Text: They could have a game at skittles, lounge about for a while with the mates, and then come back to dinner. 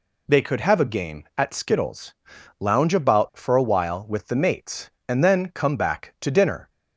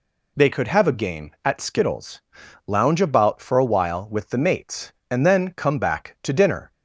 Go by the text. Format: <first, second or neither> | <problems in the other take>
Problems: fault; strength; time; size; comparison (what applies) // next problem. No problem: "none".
neither | none